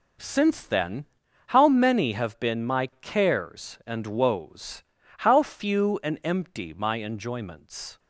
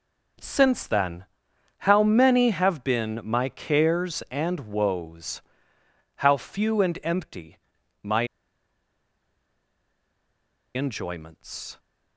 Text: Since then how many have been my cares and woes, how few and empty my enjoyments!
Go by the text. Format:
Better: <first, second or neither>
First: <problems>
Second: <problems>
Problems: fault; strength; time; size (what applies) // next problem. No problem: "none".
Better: first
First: pauses between "then" and "how"; at 1.0 s; 0.42 s long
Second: pauses between "then" and "how"; noticeable; at 1.2 s; 0.58 s long // pauses between "empty" and "my"; noticeable; at 7.5 s; 0.46 s long // pauses between "my" and "enjoyments"; strong; at 8.2 s; 2.4 s long